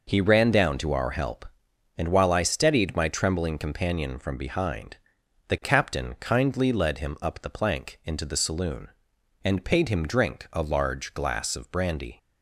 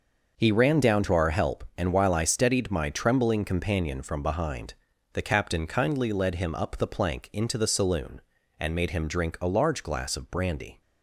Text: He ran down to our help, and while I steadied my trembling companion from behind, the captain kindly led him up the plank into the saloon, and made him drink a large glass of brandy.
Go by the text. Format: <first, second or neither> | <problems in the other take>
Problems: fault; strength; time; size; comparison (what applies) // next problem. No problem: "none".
second | says "paid" for "made"; at 9.6 s